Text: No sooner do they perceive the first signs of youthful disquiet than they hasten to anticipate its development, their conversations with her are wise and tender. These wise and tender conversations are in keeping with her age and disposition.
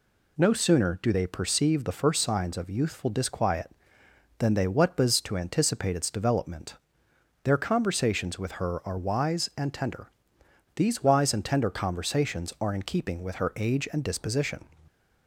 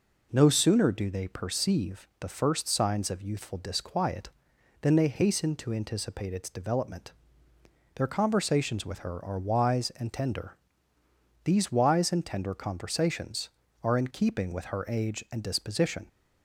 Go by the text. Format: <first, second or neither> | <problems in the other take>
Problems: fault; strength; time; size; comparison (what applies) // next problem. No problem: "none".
second | says "whatbas" for "hasten"; at 4.6 s